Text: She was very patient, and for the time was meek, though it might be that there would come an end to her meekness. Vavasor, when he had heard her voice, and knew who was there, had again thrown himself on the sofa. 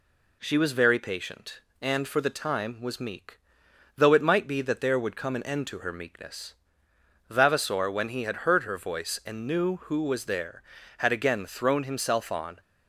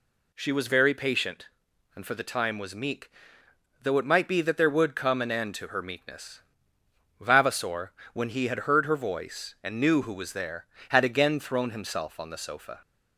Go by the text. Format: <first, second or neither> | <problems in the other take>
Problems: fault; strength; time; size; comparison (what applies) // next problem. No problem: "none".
second | stops before "the sofa"; at 12.5 s